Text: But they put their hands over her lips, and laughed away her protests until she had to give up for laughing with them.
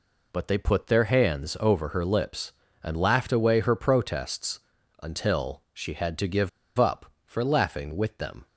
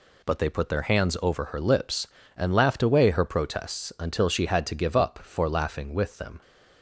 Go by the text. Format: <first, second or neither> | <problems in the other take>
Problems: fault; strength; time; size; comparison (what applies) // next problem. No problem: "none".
second | pauses between "protests" and "until"; at 4.6 s; 0.42 s long // pauses between "give" and "up"; slight; at 6.4 s; 0.29 s long